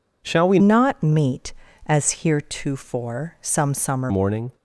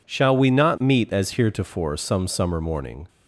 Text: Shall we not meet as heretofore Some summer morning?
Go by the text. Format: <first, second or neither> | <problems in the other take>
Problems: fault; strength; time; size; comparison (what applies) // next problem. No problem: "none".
second | changes voice from "not" to "summer"; from 0.5 to 4.1 s; 3.6 s long